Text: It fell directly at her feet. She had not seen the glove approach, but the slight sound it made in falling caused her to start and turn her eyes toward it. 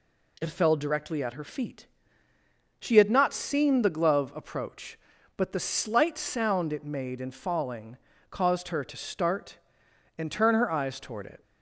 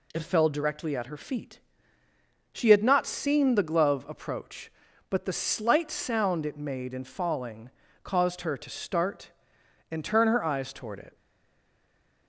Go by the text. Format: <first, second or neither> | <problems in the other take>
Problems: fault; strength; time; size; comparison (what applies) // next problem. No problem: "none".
first | pauses between "falling" and "caused"; slight; at 7.6 s; 0.34 s long; slight in the first // stays silent after the last word; noticeable; from 11.1 s on; 1.1 s long